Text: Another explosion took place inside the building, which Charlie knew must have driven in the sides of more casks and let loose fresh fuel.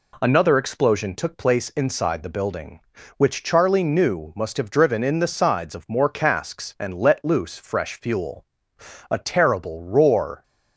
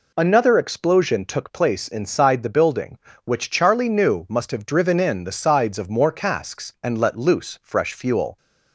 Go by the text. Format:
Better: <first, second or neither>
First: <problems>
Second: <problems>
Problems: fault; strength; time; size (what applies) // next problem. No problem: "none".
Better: second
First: goes on to say "A terrible roar"; from 9.0 s on; 1.3 s long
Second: none